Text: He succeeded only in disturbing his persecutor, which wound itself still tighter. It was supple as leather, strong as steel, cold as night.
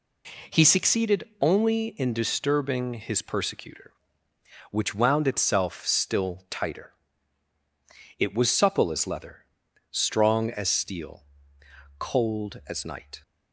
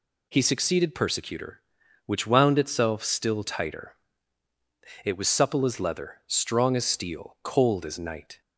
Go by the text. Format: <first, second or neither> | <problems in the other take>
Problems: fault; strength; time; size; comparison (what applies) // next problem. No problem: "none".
first | skips "only in disturbing his"; at 0.9 s